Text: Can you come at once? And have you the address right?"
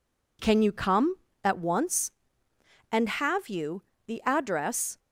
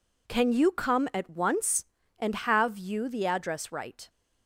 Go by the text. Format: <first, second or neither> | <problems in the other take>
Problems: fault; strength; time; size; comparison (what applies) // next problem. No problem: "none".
second | pauses between "you" and "the"; slight; at 3.8 s; 0.24 s long // stops before "right"; at 4.9 s